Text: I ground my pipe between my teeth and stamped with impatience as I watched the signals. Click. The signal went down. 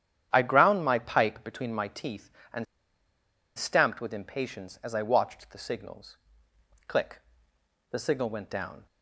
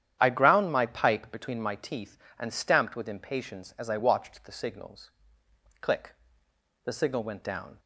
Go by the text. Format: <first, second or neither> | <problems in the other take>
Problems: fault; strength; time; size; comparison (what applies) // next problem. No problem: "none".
second | starts louder than the rest; strong; until 1.3 s; 10 dB; strong in the second // pauses between "and" and "stamped"; noticeable; at 2.6 s; 0.91 s long